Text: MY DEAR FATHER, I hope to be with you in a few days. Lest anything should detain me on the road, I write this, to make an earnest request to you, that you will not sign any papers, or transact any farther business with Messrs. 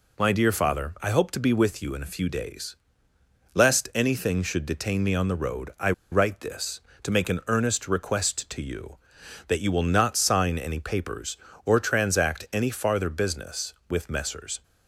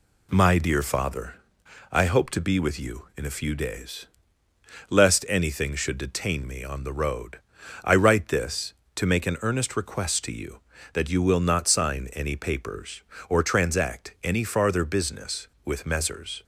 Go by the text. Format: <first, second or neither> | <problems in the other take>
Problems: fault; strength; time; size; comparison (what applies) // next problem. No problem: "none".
second | pauses between "I" and "write"; slight; at 5.9 s; 0.20 s long